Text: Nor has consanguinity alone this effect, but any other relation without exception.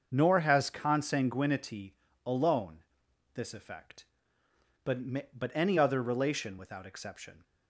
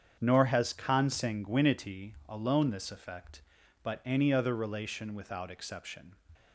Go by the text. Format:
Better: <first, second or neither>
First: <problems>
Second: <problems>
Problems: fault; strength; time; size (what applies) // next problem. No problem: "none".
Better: second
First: starts louder than the rest; until 1.1 s; 6.5 dB // pauses between "consanguinity" and "alone"; slight; at 1.9 s; 0.32 s long // pauses between "alone" and "this"; noticeable; at 2.7 s; 0.54 s long // says "but" twice; at 5.3 s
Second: starts louder than the rest; strong; until 1.2 s; 7.5 dB